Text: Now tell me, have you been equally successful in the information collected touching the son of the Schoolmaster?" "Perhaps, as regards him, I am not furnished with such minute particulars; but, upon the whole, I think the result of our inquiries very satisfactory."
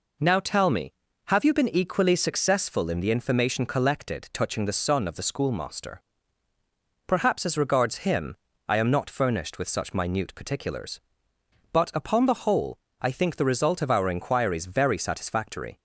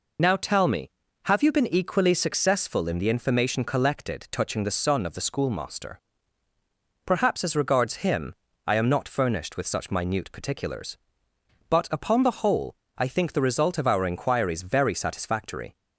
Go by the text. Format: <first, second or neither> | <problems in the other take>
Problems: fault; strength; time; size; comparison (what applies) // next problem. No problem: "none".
first | loses the start of "Now"; at 0.1 s; 30 ms